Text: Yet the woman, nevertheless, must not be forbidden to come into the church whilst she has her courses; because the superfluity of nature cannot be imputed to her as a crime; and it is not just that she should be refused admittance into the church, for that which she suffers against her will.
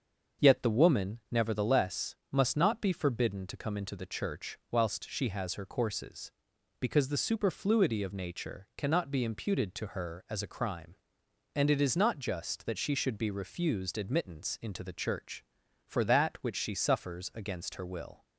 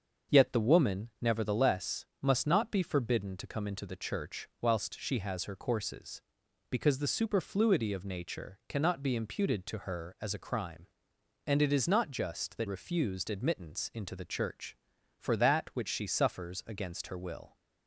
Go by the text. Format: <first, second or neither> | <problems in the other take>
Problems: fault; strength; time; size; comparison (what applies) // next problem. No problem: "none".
first | starts louder than the rest; until 1.4 s; 6.5 dB; also in the first // skips "she should be"; at 12.6 s